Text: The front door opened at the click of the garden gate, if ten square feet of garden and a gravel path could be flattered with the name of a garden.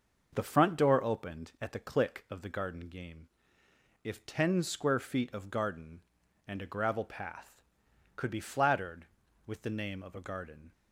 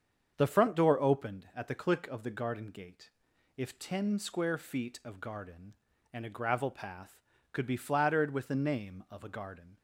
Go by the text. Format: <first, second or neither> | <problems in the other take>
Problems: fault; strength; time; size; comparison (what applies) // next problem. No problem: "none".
second | starts louder than the rest; until 1.3 s; 6 dB; strong in the second // says "game" for "gate"; at 2.8 s